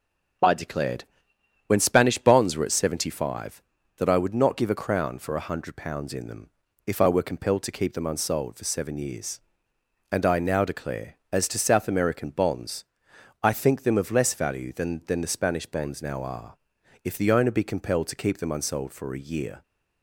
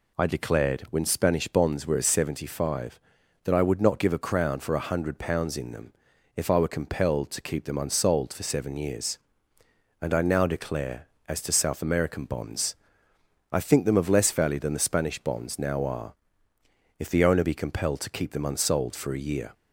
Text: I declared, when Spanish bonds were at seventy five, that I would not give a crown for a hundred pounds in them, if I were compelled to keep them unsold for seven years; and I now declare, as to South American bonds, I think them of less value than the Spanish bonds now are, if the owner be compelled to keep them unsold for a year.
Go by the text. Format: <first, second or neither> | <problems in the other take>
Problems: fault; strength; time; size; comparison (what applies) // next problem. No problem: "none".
second | starts louder than the rest; until 2.0 s; 6.5 dB // says "than" twice; at 15.0 s